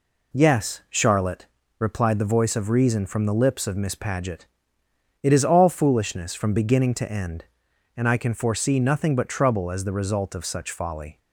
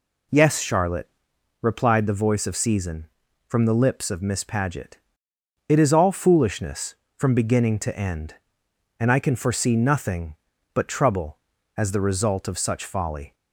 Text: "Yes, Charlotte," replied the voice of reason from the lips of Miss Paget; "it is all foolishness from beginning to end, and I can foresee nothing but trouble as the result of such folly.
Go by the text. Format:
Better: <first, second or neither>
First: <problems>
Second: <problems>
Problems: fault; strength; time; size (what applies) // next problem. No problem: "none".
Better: first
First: none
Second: says "season" for "reason"; at 2.5 s